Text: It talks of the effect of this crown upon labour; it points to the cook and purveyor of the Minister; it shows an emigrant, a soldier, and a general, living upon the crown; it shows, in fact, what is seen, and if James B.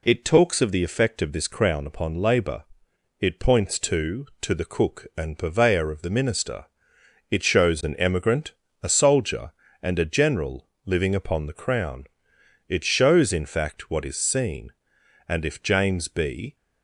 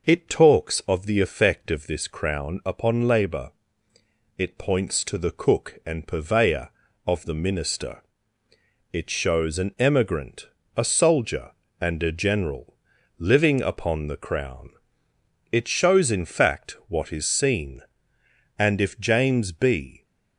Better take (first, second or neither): second